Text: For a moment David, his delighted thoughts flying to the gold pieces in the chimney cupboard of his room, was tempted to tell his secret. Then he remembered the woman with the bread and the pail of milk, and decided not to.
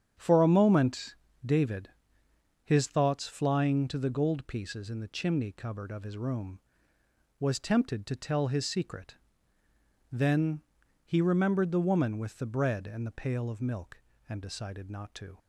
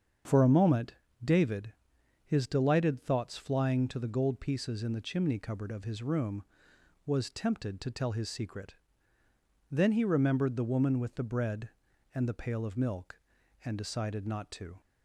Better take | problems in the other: second | starts louder than the rest; strong; until 1.5 s; 8 dB; strong in the second // pauses between "moment" and "David"; slight; at 1.1 s; 0.32 s long; slight in the second // skips "delighted"; at 2.8 s // pauses between "Then" and "he"; at 10.6 s; 0.44 s long

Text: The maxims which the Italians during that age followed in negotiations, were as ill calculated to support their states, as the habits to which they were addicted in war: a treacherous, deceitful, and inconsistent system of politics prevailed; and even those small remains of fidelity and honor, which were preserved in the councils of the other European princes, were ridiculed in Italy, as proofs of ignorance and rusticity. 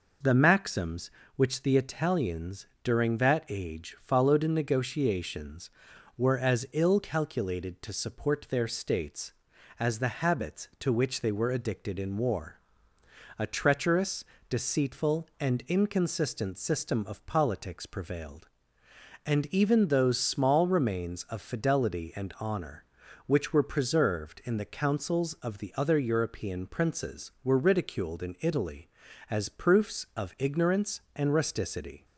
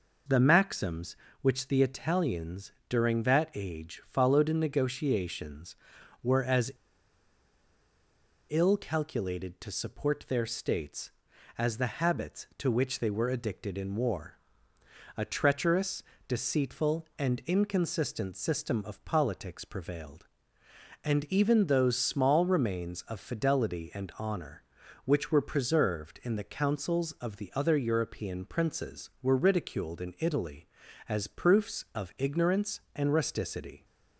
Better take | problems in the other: first | pauses between "Italians" and "during"; slight; at 2.7 s; 0.16 s long; slight in the first // pauses between "as" and "ill"; strong; at 6.7 s; 1.7 s long

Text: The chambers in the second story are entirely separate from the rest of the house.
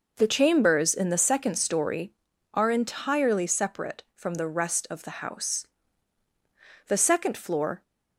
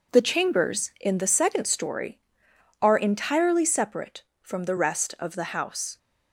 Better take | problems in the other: second | goes on to say "The second floor"; noticeable; from 6.8 s on; 0.96 s long

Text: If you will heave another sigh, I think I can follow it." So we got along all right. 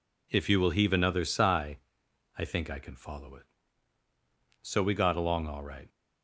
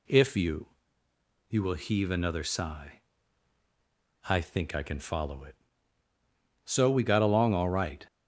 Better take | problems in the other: first | says "you" twice; at 1.4 s

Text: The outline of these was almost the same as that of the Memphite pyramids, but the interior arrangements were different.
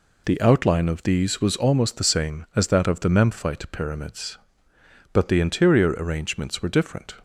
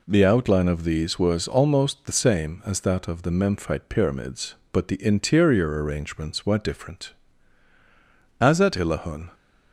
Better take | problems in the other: first | goes on to say "As at Illahun"; noticeable; from 8.3 s on; 0.96 s long

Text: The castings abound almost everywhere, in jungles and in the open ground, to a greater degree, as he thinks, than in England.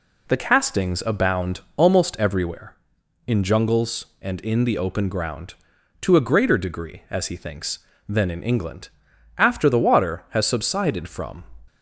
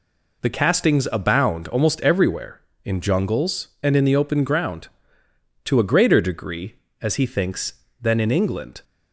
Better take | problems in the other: second | pauses between "abound" and "almost"; slight; at 1.6 s; 0.16 s long // goes on to say "After the water has subsided from"; strong; from 9.3 s on; 2.0 s long

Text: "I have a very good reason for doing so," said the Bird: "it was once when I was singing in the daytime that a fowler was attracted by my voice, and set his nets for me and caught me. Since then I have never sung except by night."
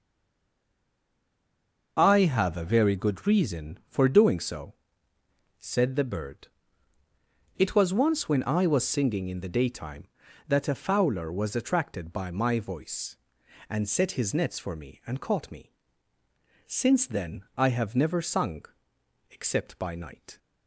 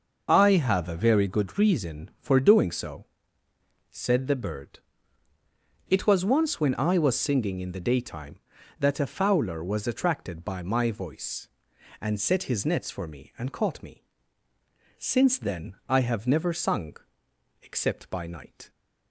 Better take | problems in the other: second | stays silent before the first word; noticeable; until 1.9 s; 1.9 s long // pauses between "sung" and "except"; noticeable; at 18.6 s; 0.62 s long; noticeable in the second

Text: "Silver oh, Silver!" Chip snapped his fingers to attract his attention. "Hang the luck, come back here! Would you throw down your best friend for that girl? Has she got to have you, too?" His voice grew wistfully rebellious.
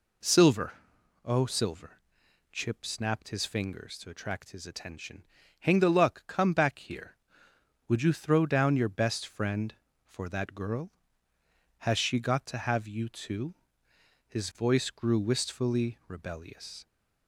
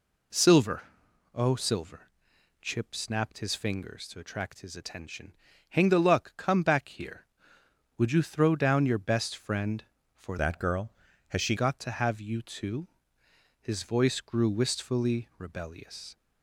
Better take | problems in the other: first | pauses between "Silver" and "oh"; noticeable; at 0.8 s; 0.52 s long; noticeable in the first // changes voice from "that" to "she"; from 10.3 to 11.5 s; 1.2 s long

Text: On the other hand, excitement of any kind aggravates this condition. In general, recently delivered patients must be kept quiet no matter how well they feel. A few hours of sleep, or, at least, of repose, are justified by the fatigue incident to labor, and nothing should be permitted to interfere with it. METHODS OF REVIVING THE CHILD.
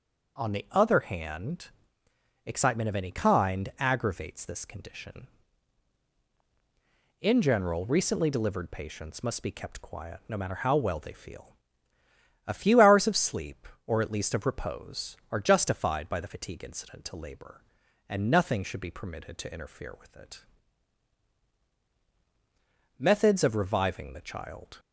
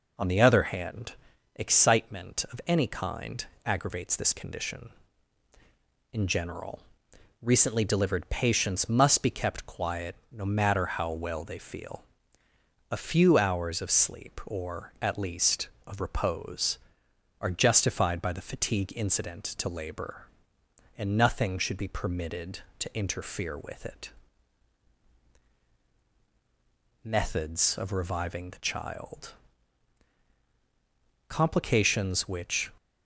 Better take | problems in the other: first | pauses between "kind" and "aggravates"; slight; at 3.4 s; 0.20 s long // pauses between "quiet" and "no"; slight; at 10.1 s; 0.16 s long // goes on to say "Complications which"; from 31.2 s on; 1.4 s long

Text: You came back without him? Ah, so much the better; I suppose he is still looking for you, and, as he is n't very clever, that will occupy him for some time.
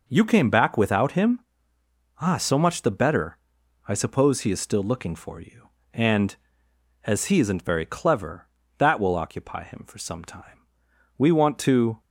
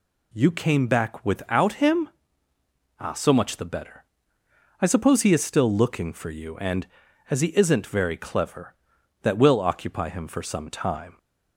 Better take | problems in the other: second | goes on to say "We want to"; noticeable; from 11.1 s on; 0.84 s long

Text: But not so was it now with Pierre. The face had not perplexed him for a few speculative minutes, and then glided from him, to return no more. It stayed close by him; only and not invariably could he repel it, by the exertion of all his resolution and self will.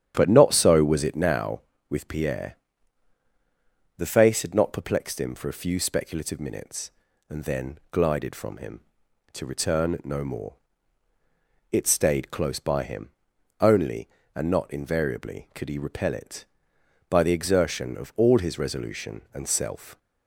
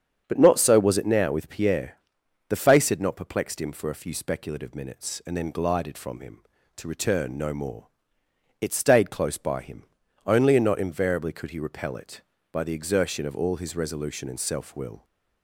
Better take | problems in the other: second | starts louder than the rest; strong; until 1.1 s; 9.5 dB; strong in the second // stops before "will"; at 19.9 s

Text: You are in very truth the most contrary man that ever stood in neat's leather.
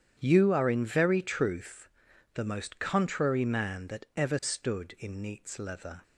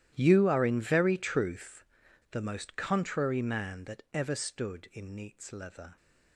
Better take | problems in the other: first | gets quieter; strong; throughout; 18.5 dB // starts louder than the rest; strong; until 1.1 s; 12.5 dB; strong in the first // pauses between "truth" and "the"; at 1.8 s; 0.45 s long; also in the first

